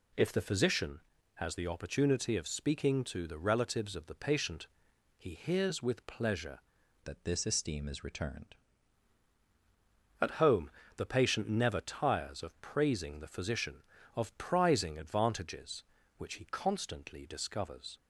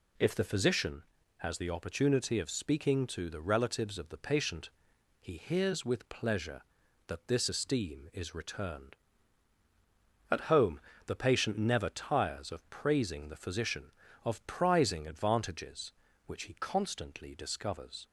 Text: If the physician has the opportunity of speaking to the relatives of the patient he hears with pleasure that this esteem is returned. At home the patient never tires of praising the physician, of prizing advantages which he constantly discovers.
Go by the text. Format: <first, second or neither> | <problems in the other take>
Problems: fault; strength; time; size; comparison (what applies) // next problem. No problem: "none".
second | pauses between "patient" and "he"; noticeable; at 4.6 s; 0.50 s long; noticeable in the second // changes voice from "that" to "returned"; from 7.0 to 8.5 s; 1.5 s long // pauses between "home" and "the"; slight; at 10.6 s; 0.28 s long; slight in the second